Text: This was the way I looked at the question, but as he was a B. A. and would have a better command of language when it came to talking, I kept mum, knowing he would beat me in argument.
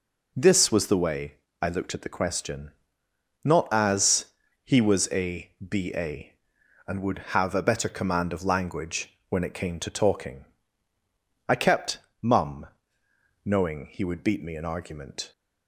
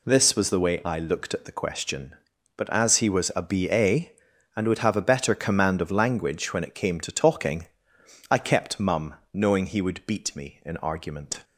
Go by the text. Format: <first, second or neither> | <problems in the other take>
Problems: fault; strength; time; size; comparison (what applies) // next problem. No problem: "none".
second | pauses between "way" and "I"; slight; at 1.3 s; 0.26 s long // says "not" for "but"; at 3.4 s // pauses between "as" and "he"; at 4.2 s; 0.38 s long // pauses between "a" and "B"; slight; at 5.5 s; 0.16 s long // pauses between "kept" and "mum"; slight; at 11.9 s; 0.24 s long